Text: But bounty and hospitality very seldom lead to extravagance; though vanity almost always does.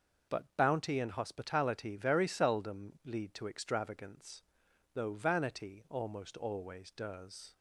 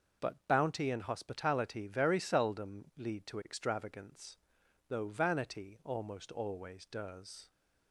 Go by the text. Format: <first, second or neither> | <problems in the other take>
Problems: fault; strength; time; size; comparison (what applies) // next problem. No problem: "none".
neither | starts louder than the rest; noticeable; the same in both